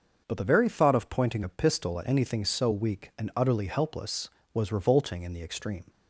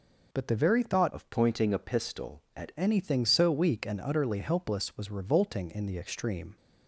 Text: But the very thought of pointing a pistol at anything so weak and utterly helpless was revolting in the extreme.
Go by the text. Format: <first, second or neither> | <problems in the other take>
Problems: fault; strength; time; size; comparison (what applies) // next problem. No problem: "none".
first | changes voice from "of" to "at"; from 1.1 to 2.7 s; 1.6 s long